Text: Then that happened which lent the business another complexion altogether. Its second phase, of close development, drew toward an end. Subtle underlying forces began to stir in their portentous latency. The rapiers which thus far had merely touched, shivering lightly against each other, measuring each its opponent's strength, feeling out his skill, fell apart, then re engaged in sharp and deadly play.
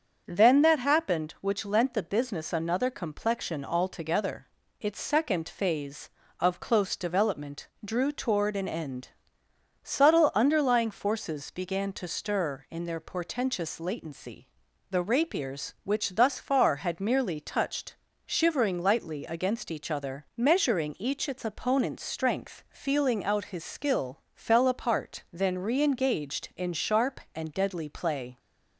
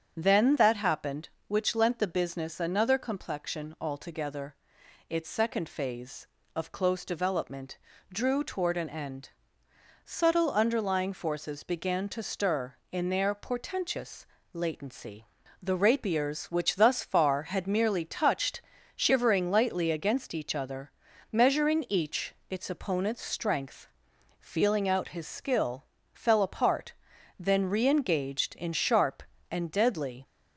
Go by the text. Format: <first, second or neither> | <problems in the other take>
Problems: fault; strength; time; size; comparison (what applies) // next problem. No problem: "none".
first | starts louder than the rest; strong; until 1.1 s; 7.5 dB; also in the first // pauses between "portentous" and "latency"; slight; at 14.2 s; 0.28 s long // stops before "play"; at 30.2 s